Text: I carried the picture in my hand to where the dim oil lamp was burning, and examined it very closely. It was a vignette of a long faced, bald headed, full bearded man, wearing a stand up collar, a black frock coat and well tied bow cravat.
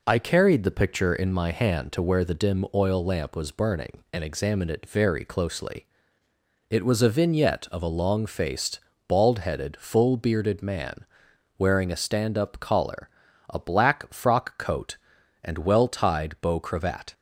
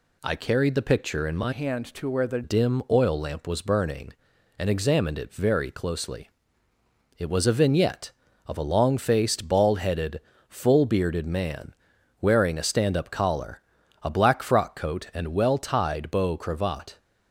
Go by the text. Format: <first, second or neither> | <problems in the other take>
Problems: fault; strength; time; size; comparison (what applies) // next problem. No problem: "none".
first | changes voice from "hand" to "the"; from 1.5 to 2.4 s; 0.9 s long